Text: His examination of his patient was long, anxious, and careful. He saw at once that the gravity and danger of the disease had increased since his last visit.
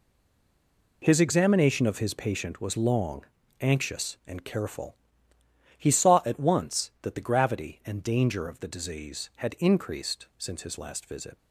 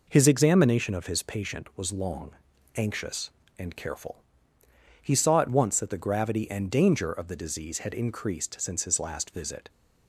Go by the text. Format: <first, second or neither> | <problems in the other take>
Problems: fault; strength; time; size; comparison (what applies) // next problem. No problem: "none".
second | stays silent before the first word; until 1.0 s; 1.0 s long